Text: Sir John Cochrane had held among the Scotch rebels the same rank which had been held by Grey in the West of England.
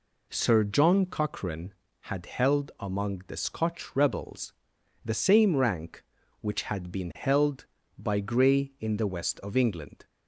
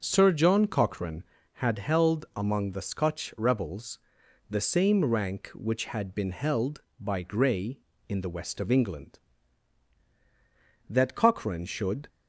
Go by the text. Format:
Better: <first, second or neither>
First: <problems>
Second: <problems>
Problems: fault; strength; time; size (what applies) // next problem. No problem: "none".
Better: first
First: pauses between "rebels" and "the"; noticeable; at 4.5 s; 0.52 s long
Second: starts louder than the rest; until 1.0 s; 6 dB // pauses between "rebels" and "the"; noticeable; at 3.9 s; 0.50 s long // goes on to say "That Cochrane should"; noticeable; from 10.8 s on; 1.2 s long